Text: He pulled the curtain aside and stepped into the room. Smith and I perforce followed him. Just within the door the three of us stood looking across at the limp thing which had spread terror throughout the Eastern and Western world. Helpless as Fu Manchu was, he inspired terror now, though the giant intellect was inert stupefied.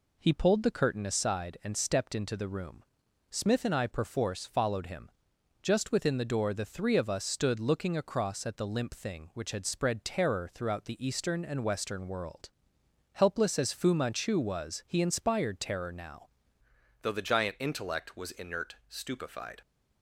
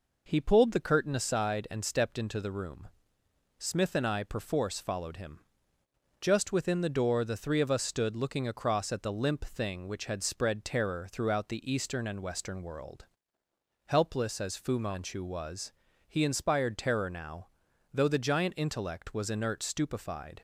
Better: second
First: changes voice at "though"; from 17.0 s on; 2.6 s long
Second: none

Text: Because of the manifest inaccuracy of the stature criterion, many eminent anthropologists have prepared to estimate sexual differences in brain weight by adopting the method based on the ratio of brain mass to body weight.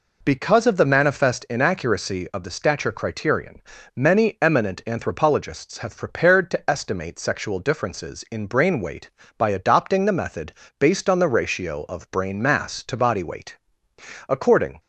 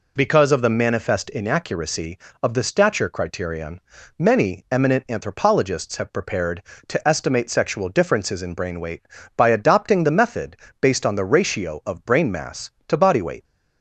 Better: second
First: pauses between "method" and "based"; slight; at 10.5 s; 0.26 s long // goes on to say "According"; from 14.2 s on; 0.52 s long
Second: pauses between "method" and "based"; slight; at 10.5 s; 0.24 s long

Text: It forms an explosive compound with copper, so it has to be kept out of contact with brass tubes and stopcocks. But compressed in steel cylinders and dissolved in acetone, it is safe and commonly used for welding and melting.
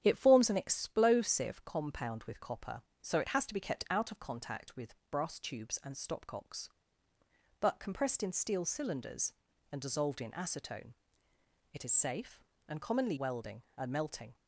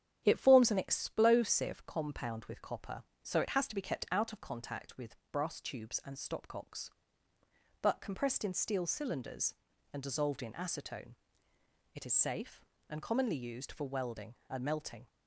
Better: second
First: starts louder than the rest; strong; until 1.0 s; 9 dB // pauses between "with" and "brass"; slight; at 4.9 s; 0.16 s long // skips "used for"; at 13.1 s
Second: starts louder than the rest; strong; until 1.2 s; 9 dB // pauses between "with" and "brass"; slight; at 5.1 s; 0.16 s long

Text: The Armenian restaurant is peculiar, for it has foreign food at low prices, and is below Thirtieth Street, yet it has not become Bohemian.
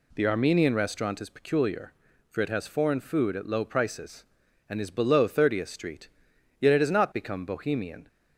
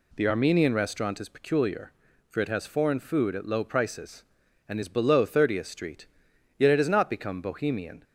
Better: neither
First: none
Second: none

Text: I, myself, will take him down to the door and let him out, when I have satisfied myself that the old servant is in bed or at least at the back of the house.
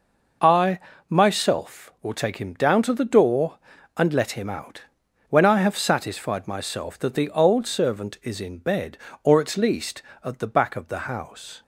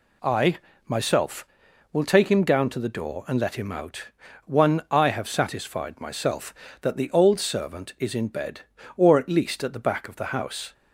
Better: first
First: none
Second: says "one" for "when"; at 4.4 s

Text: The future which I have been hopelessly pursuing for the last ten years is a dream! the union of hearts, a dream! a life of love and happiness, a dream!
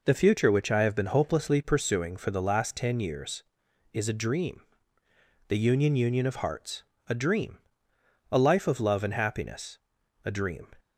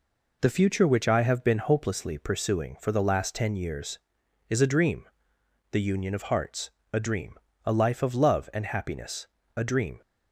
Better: second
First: says "union" twice; at 5.9 s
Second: none

